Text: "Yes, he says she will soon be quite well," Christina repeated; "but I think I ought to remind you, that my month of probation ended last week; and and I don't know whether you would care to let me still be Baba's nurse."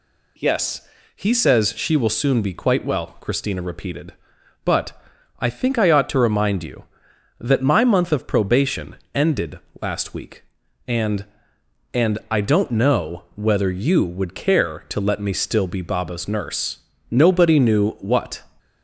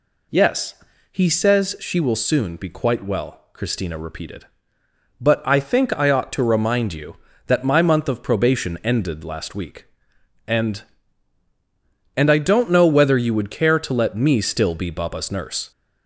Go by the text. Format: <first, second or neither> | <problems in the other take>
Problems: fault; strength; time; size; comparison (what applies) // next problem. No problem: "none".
second | pauses between "but" and "I"; noticeable; at 4.9 s; 0.48 s long // pauses between "probation" and "ended"; slight; at 8.9 s; 0.18 s long // pauses between "ended" and "last"; slight; at 9.5 s; 0.20 s long // goes on to say "Nobody knew what"; from 17.0 s on; 1.3 s long